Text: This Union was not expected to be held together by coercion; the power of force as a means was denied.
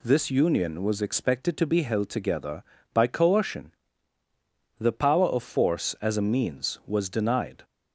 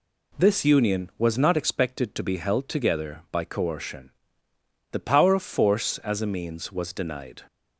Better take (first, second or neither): second